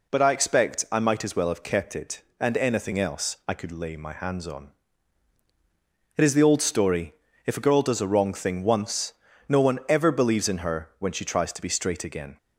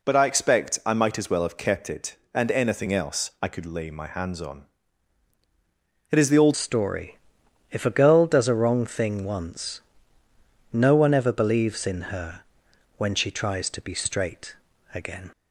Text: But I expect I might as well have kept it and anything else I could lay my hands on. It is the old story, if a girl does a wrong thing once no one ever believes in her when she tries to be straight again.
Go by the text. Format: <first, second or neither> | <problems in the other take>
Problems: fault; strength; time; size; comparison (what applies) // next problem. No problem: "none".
first | changes voice at "story"; from 6.5 s on; 8.7 s long // pauses between "once" and "no"; noticeable; at 9.8 s; 0.92 s long; slight in the first // pauses between "her" and "when"; noticeable; at 12.3 s; 0.58 s long // pauses between "straight" and "again"; at 14.5 s; 0.40 s long